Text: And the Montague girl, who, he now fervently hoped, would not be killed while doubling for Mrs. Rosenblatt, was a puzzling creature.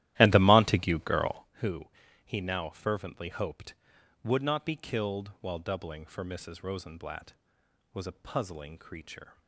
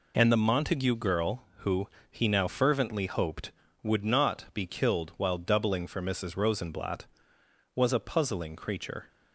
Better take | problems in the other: second | starts louder than the rest; strong; until 1.5 s; 14 dB

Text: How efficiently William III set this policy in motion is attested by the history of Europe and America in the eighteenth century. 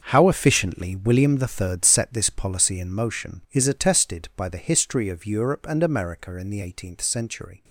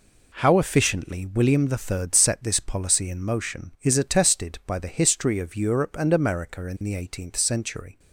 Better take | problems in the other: second | gets quieter; strong; throughout; 12.5 dB

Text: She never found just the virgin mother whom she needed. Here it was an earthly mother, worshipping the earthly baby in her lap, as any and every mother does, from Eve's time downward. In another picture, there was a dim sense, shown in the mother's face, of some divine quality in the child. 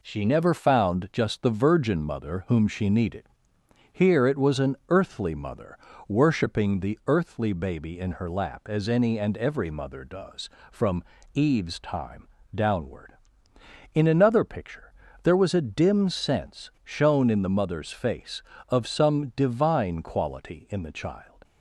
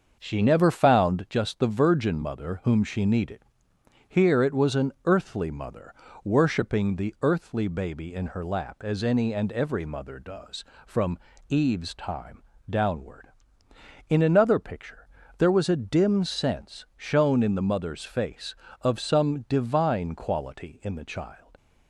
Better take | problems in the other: first | starts louder than the rest; until 1.3 s; 6.5 dB // pauses between "from" and "Eve's"; slight; at 11.1 s; 0.30 s long; slight in the first // pauses between "time" and "downward"; slight; at 12.4 s; 0.28 s long; slight in the first

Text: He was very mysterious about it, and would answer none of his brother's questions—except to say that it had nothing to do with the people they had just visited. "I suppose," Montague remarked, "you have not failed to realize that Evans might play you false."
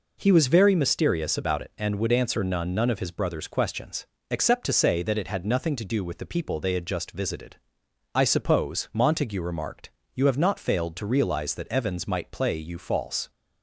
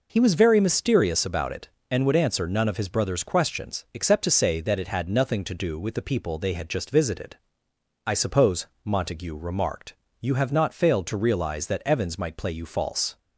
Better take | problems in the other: second | says "none" twice; at 2.7 s

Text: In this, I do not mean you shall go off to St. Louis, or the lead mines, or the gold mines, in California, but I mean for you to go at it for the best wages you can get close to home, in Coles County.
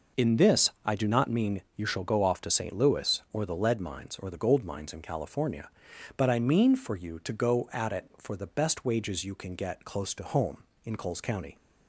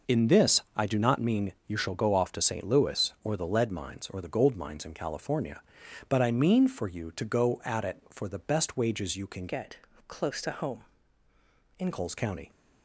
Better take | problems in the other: first | changes voice from "get" to "in"; from 9.4 to 11.9 s; 2.5 s long // pauses between "get" and "close"; slight; at 9.7 s; 0.32 s long

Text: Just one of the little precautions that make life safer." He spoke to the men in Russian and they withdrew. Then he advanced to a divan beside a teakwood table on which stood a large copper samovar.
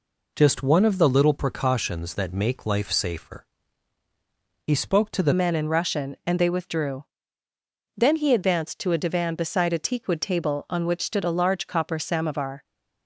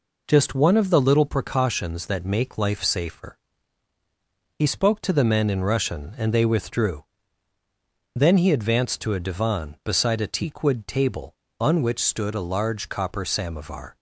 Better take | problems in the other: second | changes voice at "men"; from 5.3 s on; 7.3 s long

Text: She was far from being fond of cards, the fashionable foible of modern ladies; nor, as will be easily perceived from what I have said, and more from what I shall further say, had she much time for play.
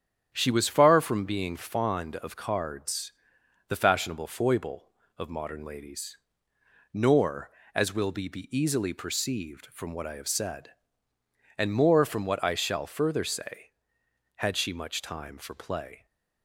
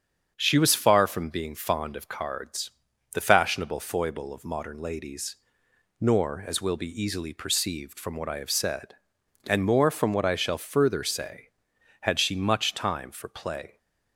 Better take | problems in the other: second | starts louder than the rest; strong; until 1.3 s; 9 dB; strong in the second // says "be" twice; at 8.2 s

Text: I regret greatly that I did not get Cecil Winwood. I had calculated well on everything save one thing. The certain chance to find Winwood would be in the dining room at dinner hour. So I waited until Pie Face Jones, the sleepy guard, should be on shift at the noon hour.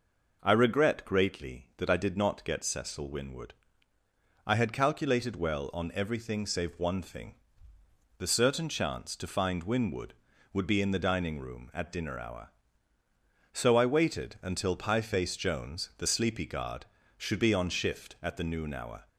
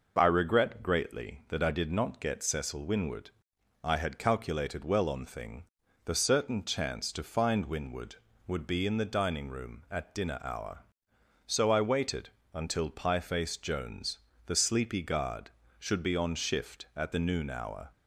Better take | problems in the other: first | skips "everything save one"; at 5.2 s // pauses between "waited" and "until"; slight; at 12.2 s; 0.26 s long

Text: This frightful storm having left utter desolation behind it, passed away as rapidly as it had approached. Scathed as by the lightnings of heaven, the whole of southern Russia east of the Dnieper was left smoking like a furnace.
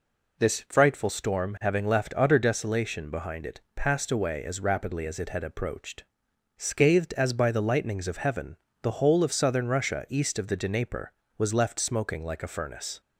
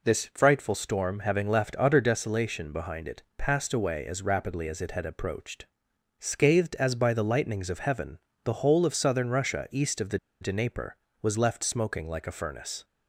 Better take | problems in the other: first | pauses between "the" and "Dnieper"; slight; at 10.1 s; 0.23 s long

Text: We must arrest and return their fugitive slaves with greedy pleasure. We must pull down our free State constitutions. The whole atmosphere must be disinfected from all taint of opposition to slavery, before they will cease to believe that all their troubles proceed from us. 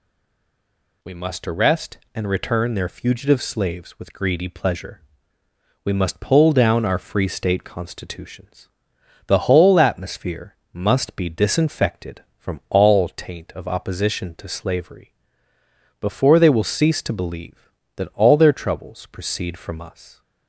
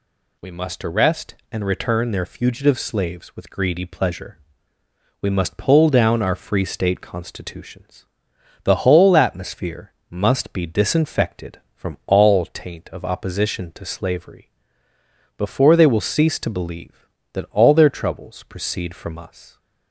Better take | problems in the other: second | stays silent before the first word; until 1.0 s; 1.0 s long // pauses between "atmosphere" and "must"; slight; at 10.5 s; 0.18 s long; slight in the second

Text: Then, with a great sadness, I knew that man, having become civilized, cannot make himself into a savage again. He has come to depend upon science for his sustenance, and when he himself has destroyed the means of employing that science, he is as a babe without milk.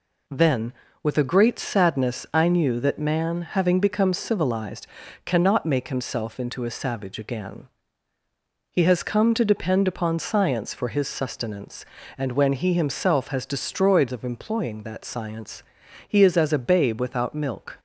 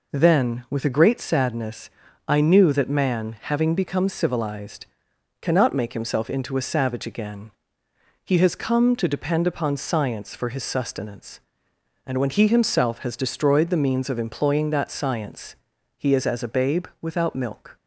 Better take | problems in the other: second | skips "the means"; at 14.1 s

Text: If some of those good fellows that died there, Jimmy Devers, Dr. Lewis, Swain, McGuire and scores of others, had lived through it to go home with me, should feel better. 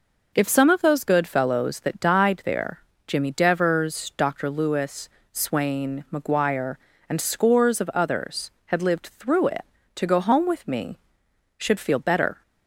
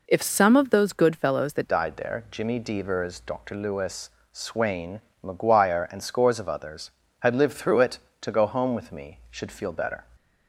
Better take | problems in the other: first | changes voice at "died"; from 1.6 s on; 8.4 s long

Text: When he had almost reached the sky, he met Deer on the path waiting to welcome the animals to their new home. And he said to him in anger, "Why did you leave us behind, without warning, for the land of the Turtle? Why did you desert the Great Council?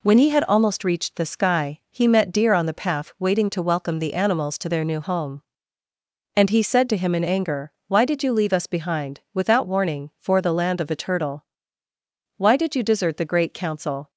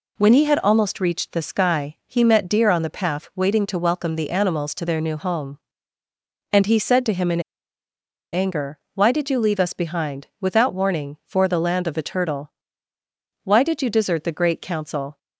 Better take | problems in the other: first | pauses between "in" and "anger"; noticeable; at 7.4 s; 0.91 s long

